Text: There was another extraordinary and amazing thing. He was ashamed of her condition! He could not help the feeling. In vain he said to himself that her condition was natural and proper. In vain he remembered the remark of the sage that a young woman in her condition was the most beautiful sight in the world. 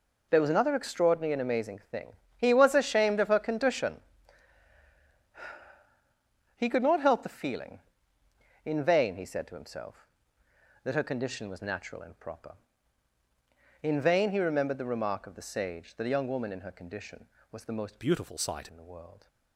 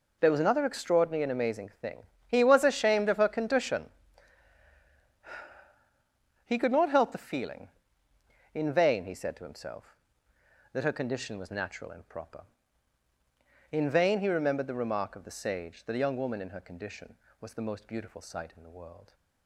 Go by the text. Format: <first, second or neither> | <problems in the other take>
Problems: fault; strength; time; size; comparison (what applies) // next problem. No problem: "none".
second | changes voice from "beautiful" to "sight"; from 17.9 to 18.6 s; 0.7 s long